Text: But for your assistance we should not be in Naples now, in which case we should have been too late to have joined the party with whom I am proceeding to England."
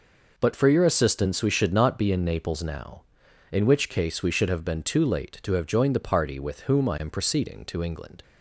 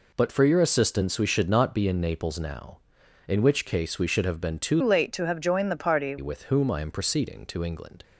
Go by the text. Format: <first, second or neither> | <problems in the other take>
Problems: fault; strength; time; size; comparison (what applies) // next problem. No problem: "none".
first | changes voice from "late" to "party"; from 4.8 to 6.1 s; 1.3 s long